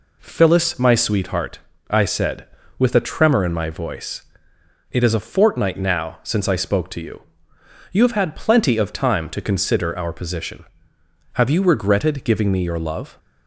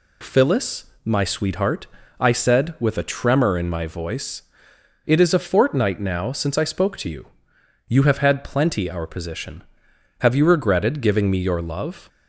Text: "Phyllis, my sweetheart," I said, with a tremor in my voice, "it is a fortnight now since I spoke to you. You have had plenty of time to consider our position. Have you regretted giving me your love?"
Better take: first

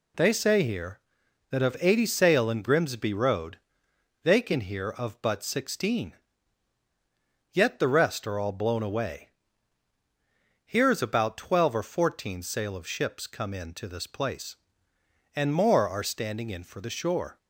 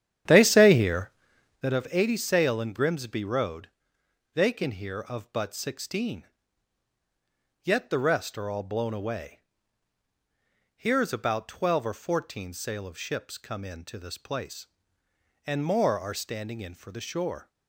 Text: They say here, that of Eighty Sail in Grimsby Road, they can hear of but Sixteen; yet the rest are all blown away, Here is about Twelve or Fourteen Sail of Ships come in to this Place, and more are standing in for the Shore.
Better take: first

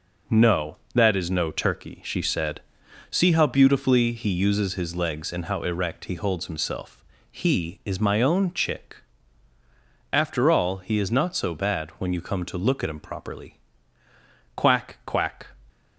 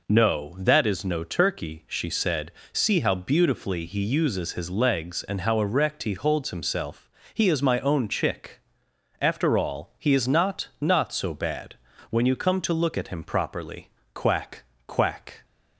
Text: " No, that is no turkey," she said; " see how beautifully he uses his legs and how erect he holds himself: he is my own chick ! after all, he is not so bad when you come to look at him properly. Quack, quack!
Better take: first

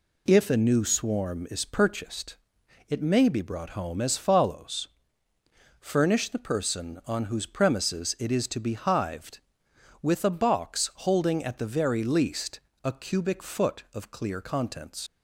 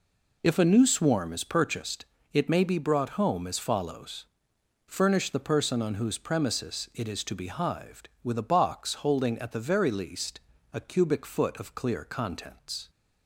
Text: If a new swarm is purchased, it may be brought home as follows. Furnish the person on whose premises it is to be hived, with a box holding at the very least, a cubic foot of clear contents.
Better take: second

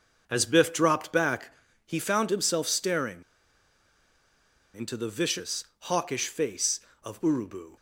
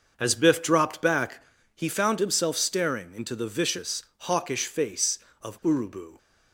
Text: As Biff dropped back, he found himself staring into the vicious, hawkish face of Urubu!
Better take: second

